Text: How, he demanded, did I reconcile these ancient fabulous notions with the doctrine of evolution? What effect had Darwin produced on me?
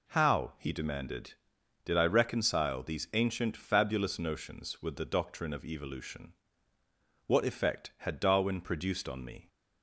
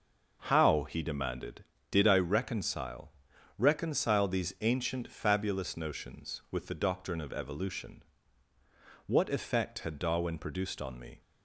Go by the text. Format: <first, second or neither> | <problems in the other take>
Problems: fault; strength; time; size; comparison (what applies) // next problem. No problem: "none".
first | says "reconcile" twice; at 3.5 s